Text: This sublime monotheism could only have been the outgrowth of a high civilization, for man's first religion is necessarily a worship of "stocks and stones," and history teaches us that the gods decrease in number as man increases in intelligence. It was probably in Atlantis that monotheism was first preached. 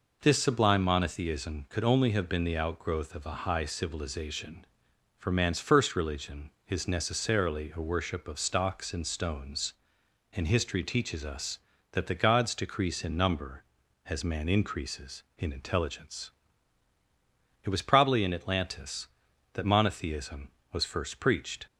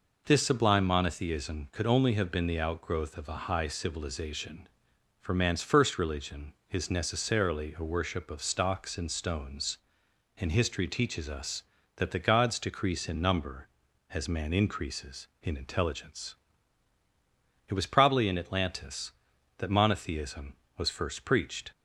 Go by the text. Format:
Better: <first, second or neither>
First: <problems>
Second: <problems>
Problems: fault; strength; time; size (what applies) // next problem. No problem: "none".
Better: neither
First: none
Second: none